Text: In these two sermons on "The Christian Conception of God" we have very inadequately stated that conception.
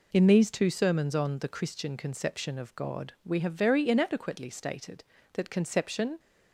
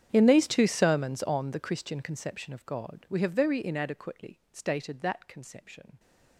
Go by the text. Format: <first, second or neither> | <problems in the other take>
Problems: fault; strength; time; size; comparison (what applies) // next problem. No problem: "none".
first | gets quieter; strong; throughout; 23.5 dB